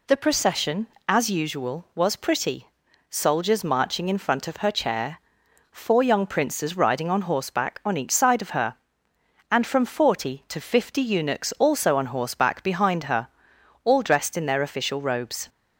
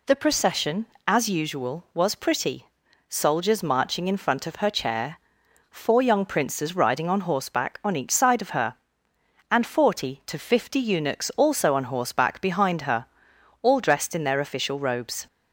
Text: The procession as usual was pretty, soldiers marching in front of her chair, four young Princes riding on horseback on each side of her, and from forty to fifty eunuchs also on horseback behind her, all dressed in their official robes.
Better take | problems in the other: first | skips "from"; at 9.6 s

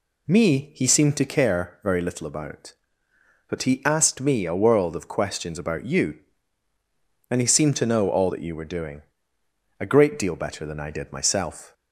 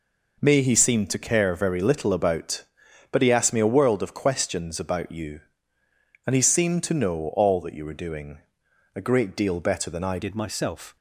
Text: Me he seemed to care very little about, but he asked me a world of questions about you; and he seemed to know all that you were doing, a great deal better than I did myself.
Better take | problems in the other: first | changes voice at "did"; from 10.2 s on; 0.7 s long

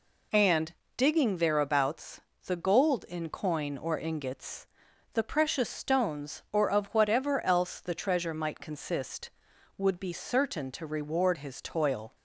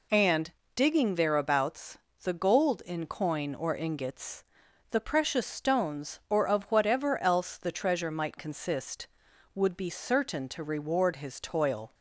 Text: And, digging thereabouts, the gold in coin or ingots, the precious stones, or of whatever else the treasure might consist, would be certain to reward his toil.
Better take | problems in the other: neither | none

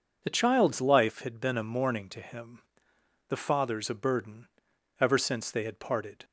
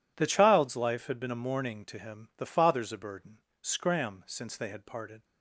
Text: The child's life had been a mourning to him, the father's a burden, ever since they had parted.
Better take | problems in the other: first | says "scram" for "ever"; at 3.6 s

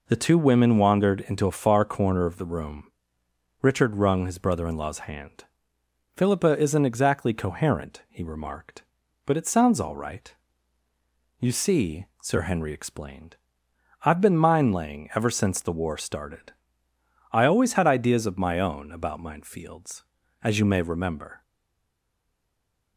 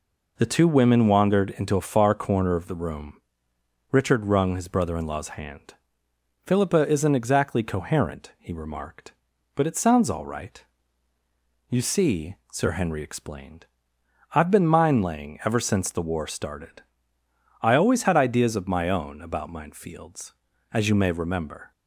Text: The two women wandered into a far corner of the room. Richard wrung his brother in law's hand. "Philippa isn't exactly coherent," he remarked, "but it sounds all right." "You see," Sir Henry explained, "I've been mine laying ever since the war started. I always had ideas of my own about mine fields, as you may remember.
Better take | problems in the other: second | stays silent after the last word; noticeable; from 21.4 s on; 1.5 s long

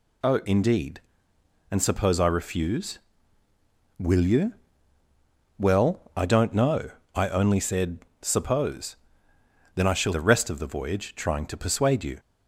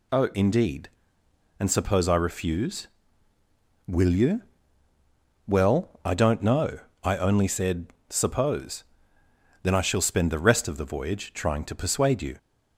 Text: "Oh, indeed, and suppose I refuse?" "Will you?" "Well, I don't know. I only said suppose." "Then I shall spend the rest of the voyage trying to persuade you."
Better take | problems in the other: second | pauses between "said" and "suppose"; slight; at 7.9 s; 0.22 s long; slight in the second // skips "spend"; at 10.1 s

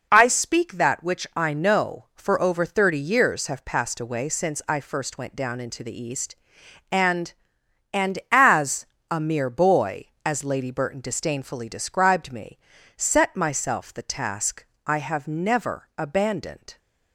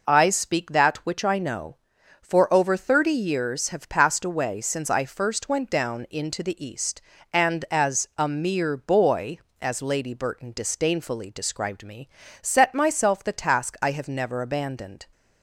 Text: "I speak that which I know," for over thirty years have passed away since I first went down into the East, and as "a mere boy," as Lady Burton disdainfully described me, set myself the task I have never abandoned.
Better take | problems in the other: second | says "and" twice; at 7.9 s // pauses between "as" and "a"; slight; at 8.8 s; 0.24 s long // pauses between "task" and "I"; slight; at 14.6 s; 0.22 s long

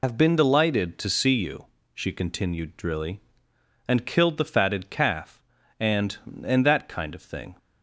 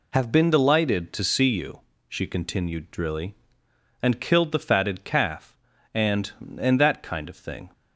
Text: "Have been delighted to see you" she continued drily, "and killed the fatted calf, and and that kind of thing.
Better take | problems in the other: second | loses the start of "Have"; at 0.0 s; 45 ms // pauses between "you" and "she"; slight; at 1.6 s; 0.26 s long; slight in the second

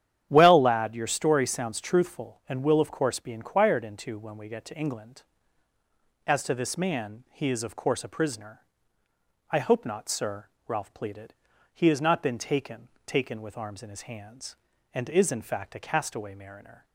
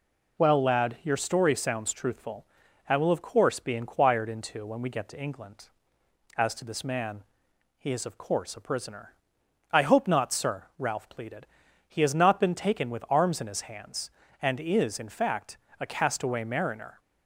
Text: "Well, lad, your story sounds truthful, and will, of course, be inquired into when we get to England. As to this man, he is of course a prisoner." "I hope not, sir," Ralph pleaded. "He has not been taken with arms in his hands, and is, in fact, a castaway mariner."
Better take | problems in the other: second | starts louder than the rest; strong; until 1.3 s; 10 dB // says "taken" twice; at 13.0 s

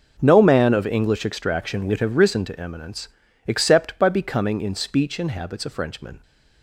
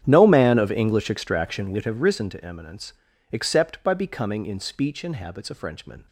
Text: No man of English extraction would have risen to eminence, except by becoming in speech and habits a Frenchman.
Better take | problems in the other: first | starts louder than the rest; strong; until 1.7 s; 9 dB

